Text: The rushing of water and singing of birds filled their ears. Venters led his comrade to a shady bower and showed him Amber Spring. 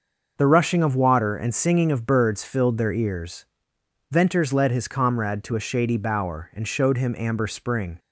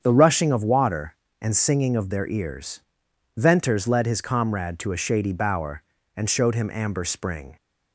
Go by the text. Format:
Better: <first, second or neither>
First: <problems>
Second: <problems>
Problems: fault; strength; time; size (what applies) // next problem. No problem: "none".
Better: first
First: starts louder than the rest; until 1.3 s; 6 dB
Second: starts louder than the rest; strong; until 1.0 s; 7.5 dB // skips "birds filled"; at 2.1 s